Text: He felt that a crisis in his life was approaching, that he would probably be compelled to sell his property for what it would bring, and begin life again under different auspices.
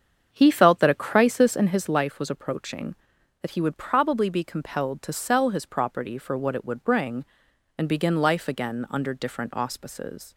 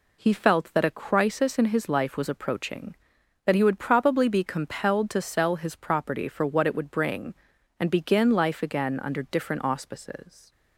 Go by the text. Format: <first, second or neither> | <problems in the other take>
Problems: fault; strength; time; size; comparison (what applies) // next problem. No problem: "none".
second | starts louder than the rest; strong; until 1.9 s; 7.5 dB